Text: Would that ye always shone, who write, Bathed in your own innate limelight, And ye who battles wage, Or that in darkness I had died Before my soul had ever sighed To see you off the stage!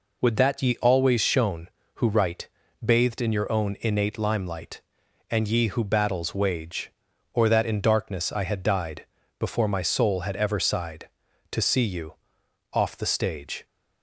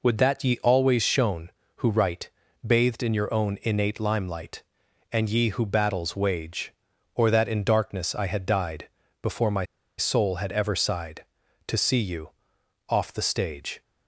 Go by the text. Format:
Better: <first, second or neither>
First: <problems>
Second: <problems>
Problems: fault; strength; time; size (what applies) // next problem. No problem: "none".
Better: first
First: pauses between "died" and "Before"; slight; at 9.0 s; 0.34 s long // pauses between "you" and "off"; noticeable; at 12.1 s; 0.58 s long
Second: pauses between "died" and "Before"; slight; at 8.8 s; 0.34 s long // pauses between "my" and "soul"; slight; at 9.6 s; 0.34 s long // pauses between "you" and "off"; noticeable; at 12.3 s; 0.58 s long